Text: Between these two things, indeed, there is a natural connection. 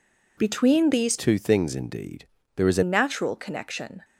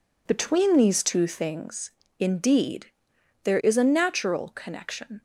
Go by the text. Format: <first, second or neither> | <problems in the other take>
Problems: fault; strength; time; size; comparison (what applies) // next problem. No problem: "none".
second | changes voice from "two" to "a"; from 1.1 to 2.8 s; 1.7 s long